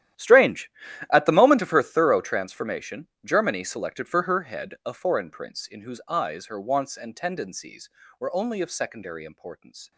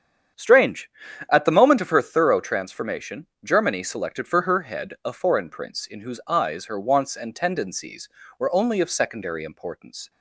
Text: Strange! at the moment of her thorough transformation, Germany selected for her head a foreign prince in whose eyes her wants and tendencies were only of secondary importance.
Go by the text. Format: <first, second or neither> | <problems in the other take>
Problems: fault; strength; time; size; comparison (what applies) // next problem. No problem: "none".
second | gets quieter; strong; throughout; 16.5 dB // starts louder than the rest; strong; until 1.5 s; 12 dB; strong in the second